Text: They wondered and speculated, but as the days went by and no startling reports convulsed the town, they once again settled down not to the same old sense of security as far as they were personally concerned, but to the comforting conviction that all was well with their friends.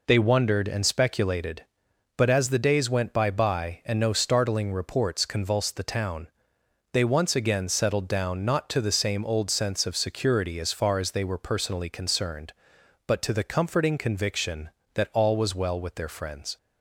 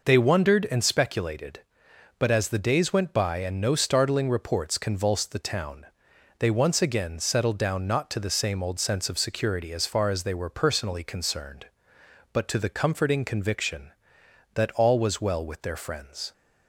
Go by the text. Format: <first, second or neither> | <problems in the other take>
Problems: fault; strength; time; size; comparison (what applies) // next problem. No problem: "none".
second | says "by" twice; at 3.3 s